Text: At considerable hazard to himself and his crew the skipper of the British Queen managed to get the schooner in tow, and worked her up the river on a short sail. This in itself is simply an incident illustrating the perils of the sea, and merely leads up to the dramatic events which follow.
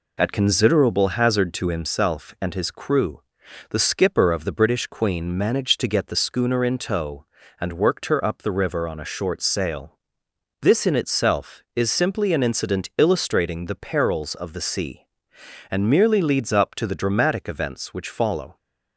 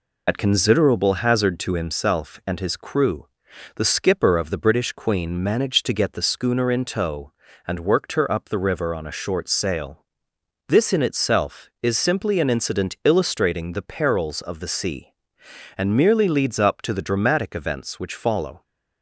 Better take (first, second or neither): first